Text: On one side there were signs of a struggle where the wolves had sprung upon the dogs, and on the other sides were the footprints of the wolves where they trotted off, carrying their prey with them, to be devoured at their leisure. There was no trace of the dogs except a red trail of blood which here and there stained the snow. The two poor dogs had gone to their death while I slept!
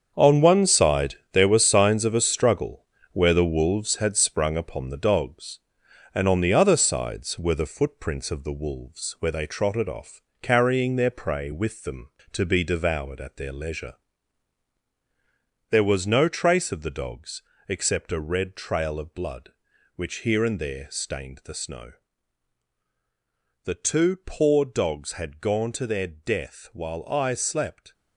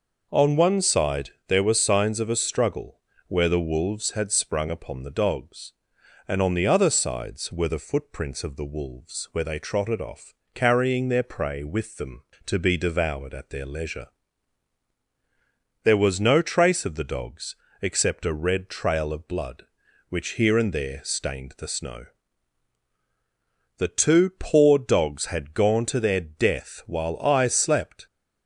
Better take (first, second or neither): second